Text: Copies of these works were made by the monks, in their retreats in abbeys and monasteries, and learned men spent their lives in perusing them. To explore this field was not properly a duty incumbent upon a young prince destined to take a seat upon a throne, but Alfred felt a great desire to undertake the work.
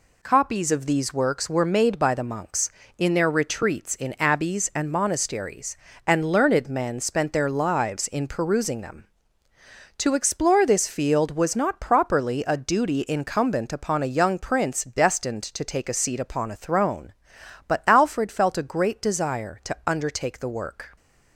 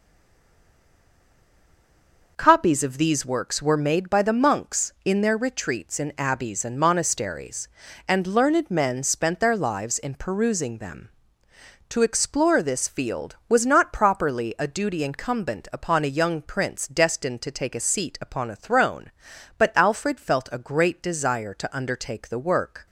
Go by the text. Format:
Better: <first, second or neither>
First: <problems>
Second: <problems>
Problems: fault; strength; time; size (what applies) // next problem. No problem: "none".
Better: first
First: none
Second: stays silent before the first word; until 2.3 s; 2.3 s long